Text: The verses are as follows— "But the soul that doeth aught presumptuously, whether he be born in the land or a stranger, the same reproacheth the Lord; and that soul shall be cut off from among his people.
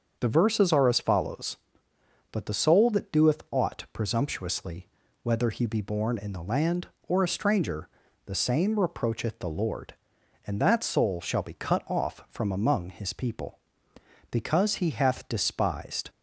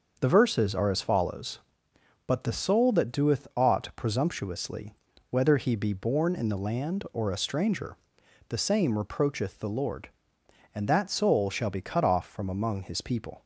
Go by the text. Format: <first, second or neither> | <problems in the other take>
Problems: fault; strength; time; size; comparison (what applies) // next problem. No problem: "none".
second | starts louder than the rest; until 1.2 s; 7 dB; also in the second // goes on to say "Because he hath despised"; strong; from 14.2 s on; 1.8 s long